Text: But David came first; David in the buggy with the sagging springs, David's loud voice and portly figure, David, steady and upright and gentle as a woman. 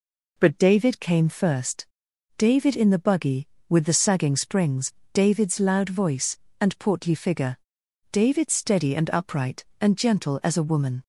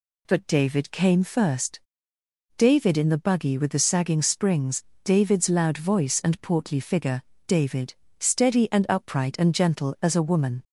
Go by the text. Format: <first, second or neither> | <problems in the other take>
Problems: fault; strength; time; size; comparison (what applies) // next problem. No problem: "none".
neither | none